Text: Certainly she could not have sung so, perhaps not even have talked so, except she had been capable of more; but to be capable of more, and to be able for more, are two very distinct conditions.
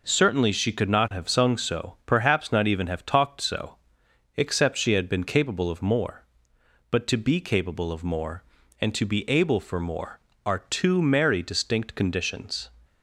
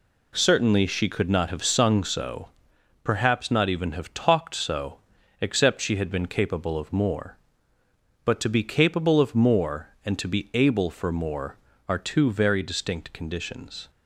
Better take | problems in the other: second | says "merry" for "very"; at 11.0 s

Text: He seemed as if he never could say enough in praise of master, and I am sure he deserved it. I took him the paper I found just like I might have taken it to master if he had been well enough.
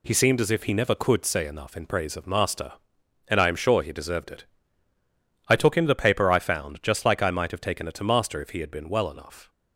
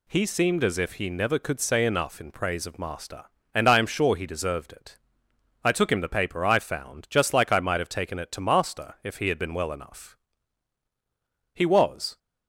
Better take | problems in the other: first | goes on to say "He was"; noticeable; from 11.5 s on; 0.64 s long

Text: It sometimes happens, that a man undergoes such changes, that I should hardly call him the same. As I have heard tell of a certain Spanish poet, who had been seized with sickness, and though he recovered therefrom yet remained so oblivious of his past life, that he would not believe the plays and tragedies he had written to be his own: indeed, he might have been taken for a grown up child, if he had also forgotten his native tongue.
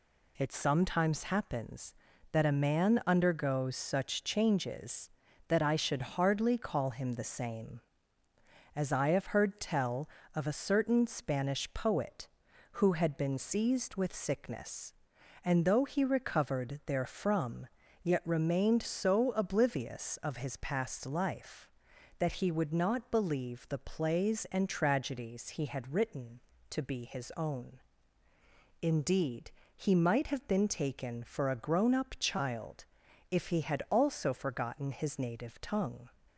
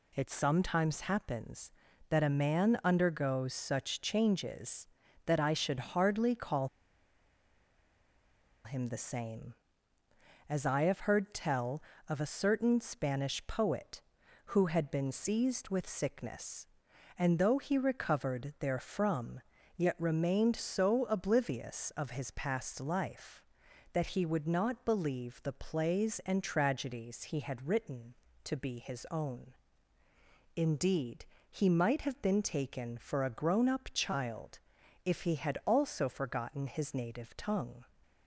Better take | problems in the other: first | pauses between "call" and "him"; strong; at 6.6 s; 1.9 s long // pauses between "therefrom" and "yet"; slight; at 19.4 s; 0.34 s long; slight in the first

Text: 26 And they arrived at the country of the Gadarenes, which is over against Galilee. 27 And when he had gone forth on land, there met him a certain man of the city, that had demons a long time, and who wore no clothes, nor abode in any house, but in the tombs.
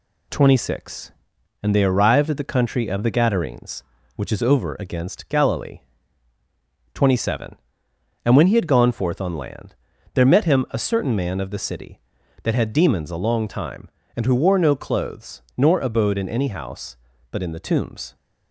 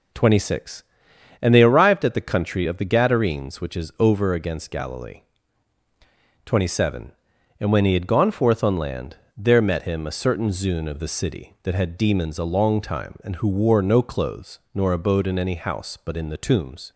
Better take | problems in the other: first | says "zune" for "man"; at 10.4 s

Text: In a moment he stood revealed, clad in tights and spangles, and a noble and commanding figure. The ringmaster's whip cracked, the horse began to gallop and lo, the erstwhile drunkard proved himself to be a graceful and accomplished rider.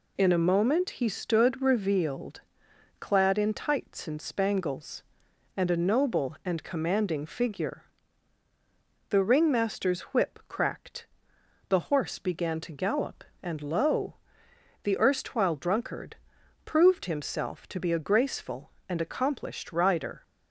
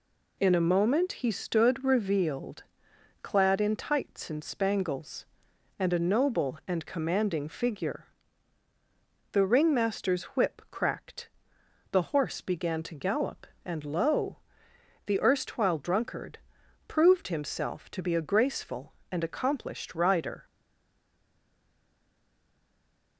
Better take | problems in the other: first | pauses between "drunkard" and "proved"; noticeable; at 16.3 s; 0.50 s long; noticeable in the first // stays silent after the last word; strong; from 20.4 s on; 2.7 s long

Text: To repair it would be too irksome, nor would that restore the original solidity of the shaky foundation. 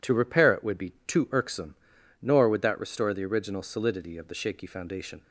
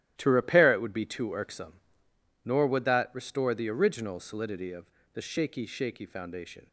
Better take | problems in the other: first | starts louder than the rest; strong; until 1.1 s; 14 dB // pauses between "of" and "the"; slight; at 4.8 s; 0.28 s long // says "shaky" twice; at 5.6 s

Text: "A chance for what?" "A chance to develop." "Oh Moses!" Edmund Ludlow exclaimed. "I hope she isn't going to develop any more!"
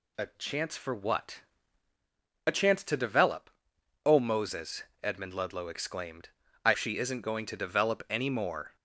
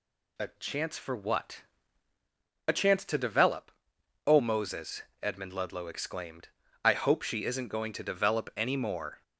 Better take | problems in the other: second | skips "hope"; at 6.7 s

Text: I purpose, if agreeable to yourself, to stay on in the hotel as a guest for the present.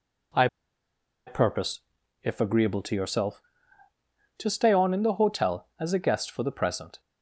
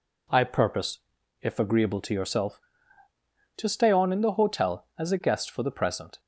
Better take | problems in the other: second | pauses between "I" and "purpose"; noticeable; at 0.4 s; 0.80 s long

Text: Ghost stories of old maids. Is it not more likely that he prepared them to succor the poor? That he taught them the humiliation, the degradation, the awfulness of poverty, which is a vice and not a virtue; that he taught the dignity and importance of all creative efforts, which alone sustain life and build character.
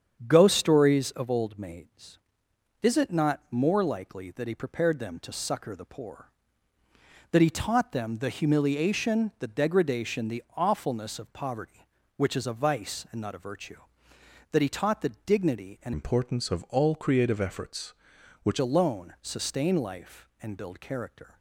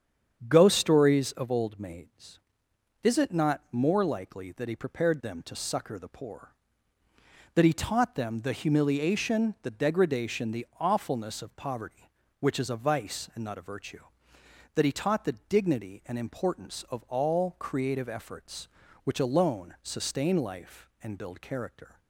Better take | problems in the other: second | starts louder than the rest; strong; until 1.2 s; 8 dB; strong in the second // changes voice from "importance" to "which"; from 15.9 to 18.5 s; 2.6 s long

